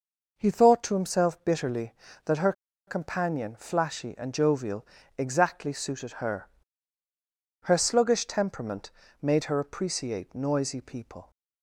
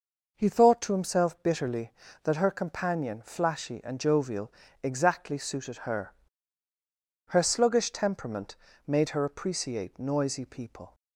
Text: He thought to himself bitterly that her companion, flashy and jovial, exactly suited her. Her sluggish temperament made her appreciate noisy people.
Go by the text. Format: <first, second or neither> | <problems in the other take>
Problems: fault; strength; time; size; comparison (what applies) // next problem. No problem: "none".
second | pauses between "her" and "companion"; slight; at 2.5 s; 0.35 s long // pauses between "temperament" and "made"; slight; at 8.9 s; 0.32 s long; slight in the second